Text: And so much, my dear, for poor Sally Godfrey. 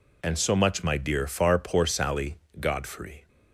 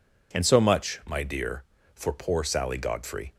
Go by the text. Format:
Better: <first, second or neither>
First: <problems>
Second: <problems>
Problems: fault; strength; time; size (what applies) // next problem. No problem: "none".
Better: second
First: says "far" for "for"; at 1.2 s // pauses between "Sally" and "Godfrey"; slight; at 2.3 s; 0.22 s long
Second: none